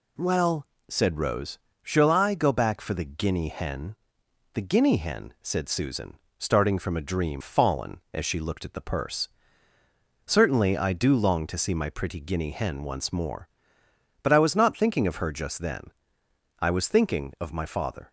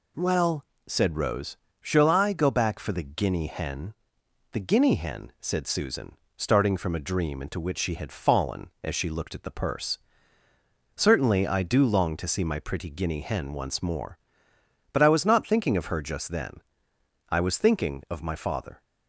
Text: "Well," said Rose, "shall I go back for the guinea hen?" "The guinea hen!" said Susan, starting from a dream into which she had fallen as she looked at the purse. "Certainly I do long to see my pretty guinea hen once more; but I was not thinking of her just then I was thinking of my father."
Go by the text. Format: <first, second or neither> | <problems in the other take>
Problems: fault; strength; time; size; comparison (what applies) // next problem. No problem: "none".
second | skips "into which she had"; at 7.4 s // pauses between "then" and "I"; noticeable; at 15.9 s; 0.68 s long; noticeable in the second